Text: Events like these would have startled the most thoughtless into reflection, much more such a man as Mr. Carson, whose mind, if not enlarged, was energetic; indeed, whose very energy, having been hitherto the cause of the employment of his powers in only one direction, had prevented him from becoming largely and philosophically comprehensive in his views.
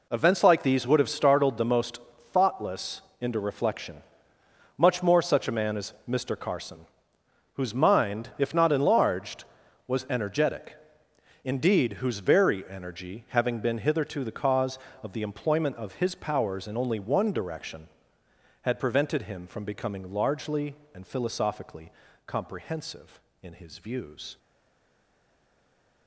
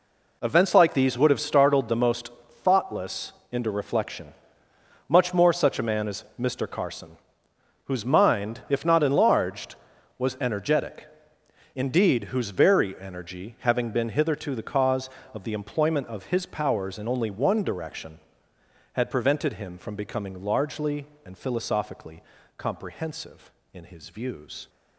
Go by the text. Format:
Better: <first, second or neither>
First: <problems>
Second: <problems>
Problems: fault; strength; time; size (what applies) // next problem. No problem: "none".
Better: second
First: pauses between "most" and "thoughtless"; slight; at 2.0 s; 0.32 s long // pauses between "thoughtless" and "into"; slight; at 3.0 s; 0.18 s long // pauses between "philosophically" and "comprehensive"; slight; at 21.9 s; 0.34 s long // stays silent after the last word; noticeable; from 24.3 s on; 1.7 s long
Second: pauses between "most" and "thoughtless"; slight; at 2.3 s; 0.32 s long // pauses between "thoughtless" and "into"; slight; at 3.3 s; 0.18 s long // pauses between "philosophically" and "comprehensive"; slight; at 22.2 s; 0.34 s long